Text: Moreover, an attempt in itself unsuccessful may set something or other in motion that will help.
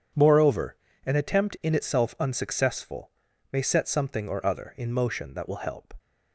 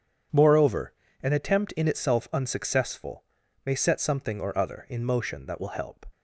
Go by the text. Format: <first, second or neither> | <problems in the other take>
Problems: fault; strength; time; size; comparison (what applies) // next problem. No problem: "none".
neither | pauses between "unsuccessful" and "may"; the same in both